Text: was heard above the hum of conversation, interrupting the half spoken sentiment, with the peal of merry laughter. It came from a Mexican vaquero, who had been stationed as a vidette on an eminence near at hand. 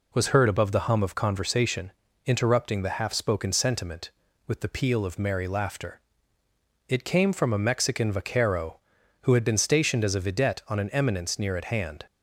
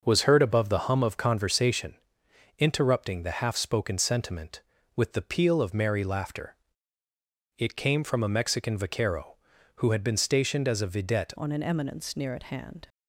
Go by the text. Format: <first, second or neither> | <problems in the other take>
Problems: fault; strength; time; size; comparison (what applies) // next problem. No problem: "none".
first | starts louder than the rest; noticeable; until 1.0 s; 6 dB // changes voice at "on"; from 11.3 s on; 1.5 s long